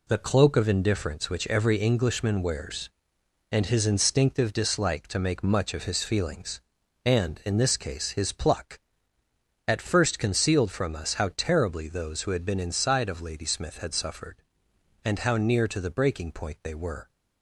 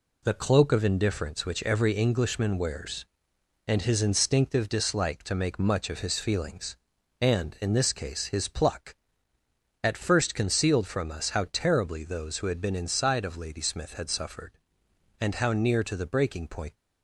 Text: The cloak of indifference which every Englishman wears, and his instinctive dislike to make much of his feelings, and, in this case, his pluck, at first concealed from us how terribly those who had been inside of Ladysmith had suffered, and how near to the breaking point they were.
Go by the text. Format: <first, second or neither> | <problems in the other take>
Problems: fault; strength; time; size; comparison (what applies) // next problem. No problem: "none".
first | stops before "they were"; at 16.7 s